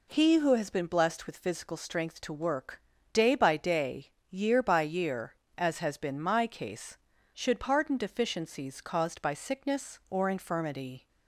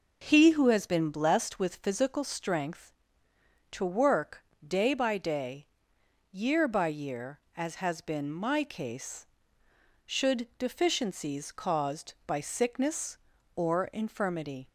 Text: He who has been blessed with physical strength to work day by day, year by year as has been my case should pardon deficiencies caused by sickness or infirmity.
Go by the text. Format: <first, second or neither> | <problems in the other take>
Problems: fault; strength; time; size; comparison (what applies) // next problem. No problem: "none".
first | pauses between "work" and "day"; slight; at 4.4 s; 0.22 s long; slight in the first // skips "pardon"; at 10.5 s